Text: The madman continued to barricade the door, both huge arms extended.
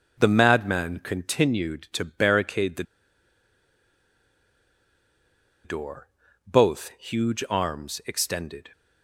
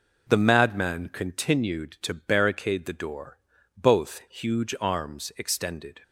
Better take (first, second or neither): second